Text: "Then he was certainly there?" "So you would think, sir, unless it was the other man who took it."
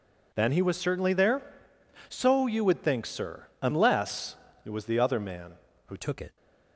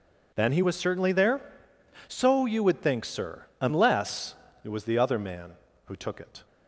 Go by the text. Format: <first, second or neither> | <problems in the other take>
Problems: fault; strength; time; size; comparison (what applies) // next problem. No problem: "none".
second | pauses between "unless" and "it"; slight; at 4.3 s; 0.28 s long; slight in the second // changes voice at "took"; from 5.9 s on; 0.4 s long